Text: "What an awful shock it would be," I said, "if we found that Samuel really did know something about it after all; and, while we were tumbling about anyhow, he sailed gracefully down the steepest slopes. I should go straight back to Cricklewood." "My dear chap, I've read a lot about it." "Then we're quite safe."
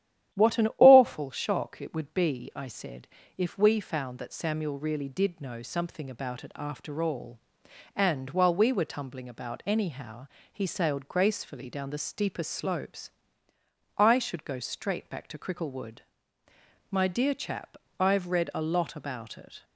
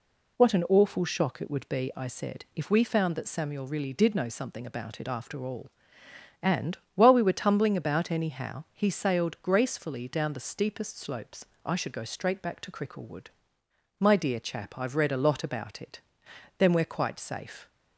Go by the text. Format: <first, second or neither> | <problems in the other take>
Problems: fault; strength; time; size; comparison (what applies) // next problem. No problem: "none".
second | starts louder than the rest; strong; until 1.4 s; 11.5 dB // stops before "Then we're quite safe"; at 19.6 s